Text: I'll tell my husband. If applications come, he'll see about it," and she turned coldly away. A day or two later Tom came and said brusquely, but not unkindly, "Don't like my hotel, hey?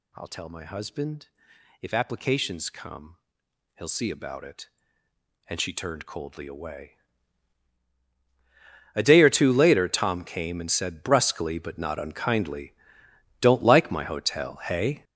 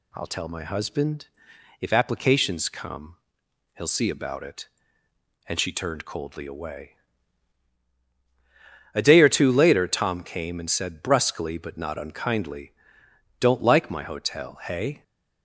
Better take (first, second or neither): second